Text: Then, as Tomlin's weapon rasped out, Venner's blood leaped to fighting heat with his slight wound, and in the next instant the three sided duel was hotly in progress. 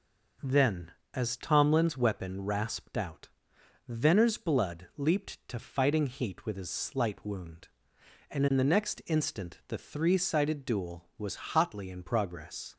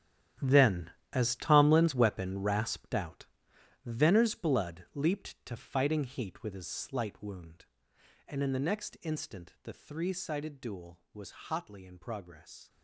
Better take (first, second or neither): first